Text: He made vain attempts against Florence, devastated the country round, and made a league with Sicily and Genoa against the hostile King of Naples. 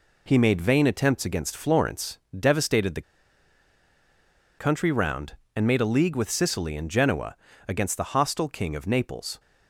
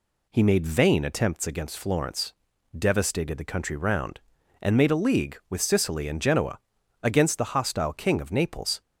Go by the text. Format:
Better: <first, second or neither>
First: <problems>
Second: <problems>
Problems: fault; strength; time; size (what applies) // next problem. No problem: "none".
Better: second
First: pauses between "the" and "country"; strong; at 3.0 s; 1.5 s long // pauses between "Genoa" and "against"; slight; at 7.3 s; 0.34 s long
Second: pauses between "Genoa" and "against"; at 6.5 s; 0.44 s long